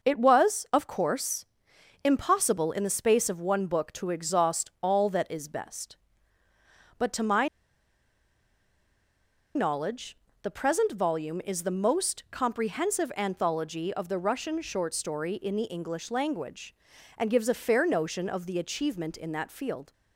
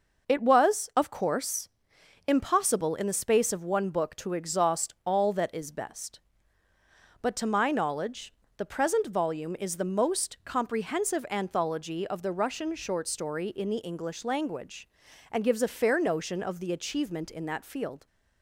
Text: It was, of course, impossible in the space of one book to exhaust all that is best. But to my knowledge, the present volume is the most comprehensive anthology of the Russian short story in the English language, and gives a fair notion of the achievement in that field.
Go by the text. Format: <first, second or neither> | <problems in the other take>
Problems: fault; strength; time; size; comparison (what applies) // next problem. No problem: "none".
second | pauses between "my" and "knowledge"; strong; at 7.4 s; 2.0 s long